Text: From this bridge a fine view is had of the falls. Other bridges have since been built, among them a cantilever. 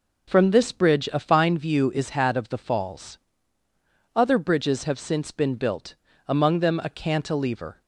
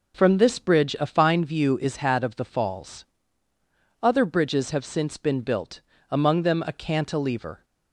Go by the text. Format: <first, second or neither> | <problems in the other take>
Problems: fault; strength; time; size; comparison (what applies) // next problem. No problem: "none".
neither | none